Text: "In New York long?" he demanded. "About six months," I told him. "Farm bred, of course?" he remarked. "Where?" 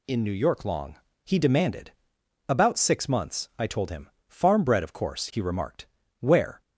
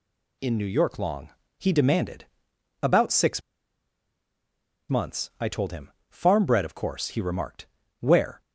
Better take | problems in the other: first | pauses between "six" and "months"; strong; at 3.4 s; 1.4 s long

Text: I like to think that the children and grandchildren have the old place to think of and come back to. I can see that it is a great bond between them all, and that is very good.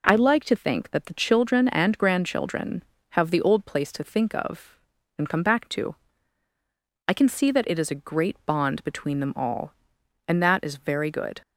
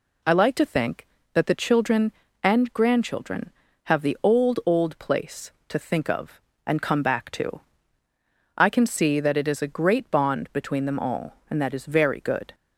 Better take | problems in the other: first | says "old" twice; at 4.6 s

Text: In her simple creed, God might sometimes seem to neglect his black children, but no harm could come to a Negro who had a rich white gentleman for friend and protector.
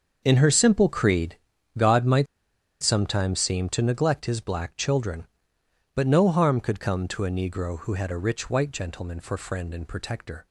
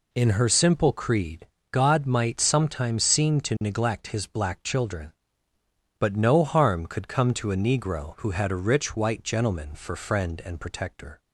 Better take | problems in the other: second | starts louder than the rest; until 1.2 s; 6.5 dB // pauses between "might" and "sometimes"; noticeable; at 2.2 s; 0.57 s long

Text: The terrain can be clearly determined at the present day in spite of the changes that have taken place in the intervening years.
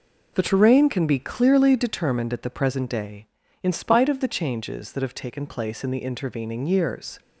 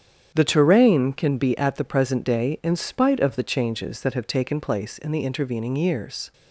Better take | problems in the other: first | starts louder than the rest; strong; until 1.3 s; 8.5 dB // skips "clearly determined"; at 1.5 s

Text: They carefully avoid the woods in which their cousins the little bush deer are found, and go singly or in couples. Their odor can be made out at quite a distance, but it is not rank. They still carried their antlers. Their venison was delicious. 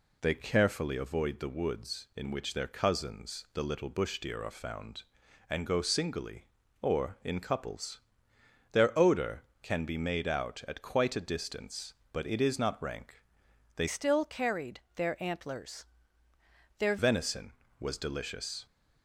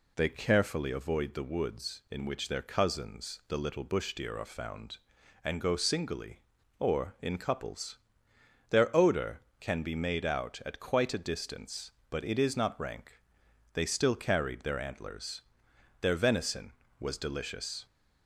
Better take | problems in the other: second | changes voice from "still" to "Their"; from 13.8 to 16.9 s; 3.1 s long // pauses between "carried" and "their"; slight; at 14.8 s; 0.16 s long

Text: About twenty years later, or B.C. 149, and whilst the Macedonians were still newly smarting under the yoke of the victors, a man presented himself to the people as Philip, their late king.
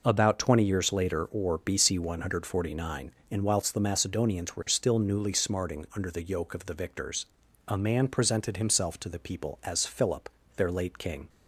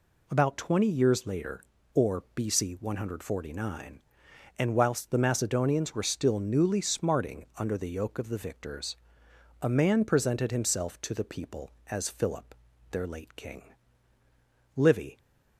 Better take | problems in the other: first | goes on to say "Livy"; slight; from 14.7 s on; 0.44 s long

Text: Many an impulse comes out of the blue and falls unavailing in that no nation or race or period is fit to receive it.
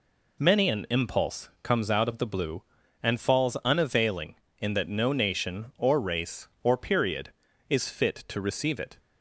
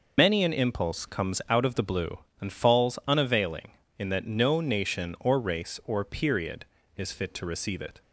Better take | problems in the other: first | loses the start of "Many"; at 0.1 s; 105 ms

